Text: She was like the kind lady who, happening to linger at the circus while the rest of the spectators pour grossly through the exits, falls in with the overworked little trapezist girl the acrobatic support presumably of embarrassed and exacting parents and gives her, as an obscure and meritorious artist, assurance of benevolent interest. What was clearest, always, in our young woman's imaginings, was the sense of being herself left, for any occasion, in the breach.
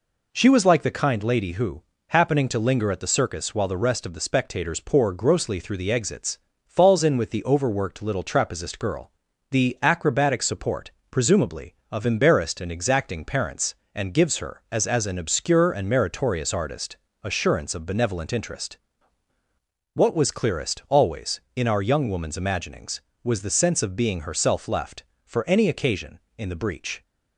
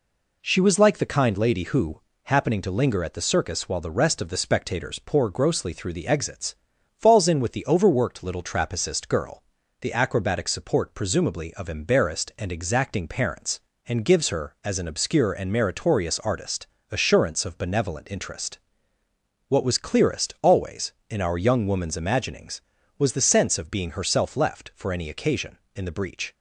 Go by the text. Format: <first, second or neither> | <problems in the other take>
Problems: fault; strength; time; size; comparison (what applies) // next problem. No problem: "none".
second | pauses between "girl" and "the"; at 9.0 s; 0.40 s long; also in the second // pauses between "support" and "presumably"; slight; at 10.9 s; 0.18 s long // says "as" twice; at 14.8 s